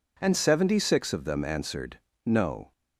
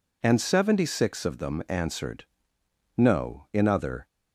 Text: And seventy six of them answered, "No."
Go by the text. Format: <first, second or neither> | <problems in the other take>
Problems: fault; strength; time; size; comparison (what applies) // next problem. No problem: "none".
first | goes on to say "In other"; from 3.5 s on; 0.54 s long